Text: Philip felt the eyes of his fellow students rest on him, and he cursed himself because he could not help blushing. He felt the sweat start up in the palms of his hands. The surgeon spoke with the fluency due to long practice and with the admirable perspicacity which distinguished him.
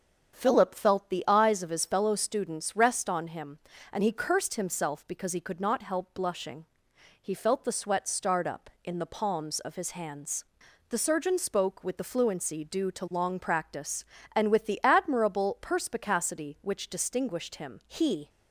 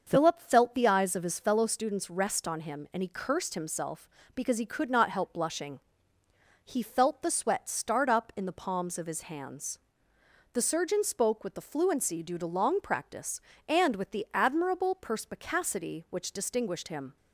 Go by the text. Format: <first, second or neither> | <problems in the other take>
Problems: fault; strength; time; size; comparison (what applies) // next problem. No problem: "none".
second | starts louder than the rest; until 1.3 s; 7 dB; also in the second // goes on to say "He"; slight; from 17.8 s on; 0.42 s long